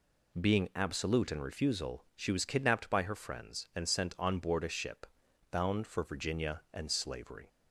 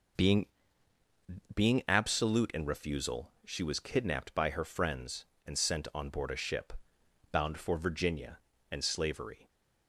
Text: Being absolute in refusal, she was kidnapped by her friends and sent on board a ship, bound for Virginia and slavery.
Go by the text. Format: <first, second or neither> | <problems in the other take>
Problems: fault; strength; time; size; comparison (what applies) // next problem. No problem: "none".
first | says "Being" twice; at 1.5 s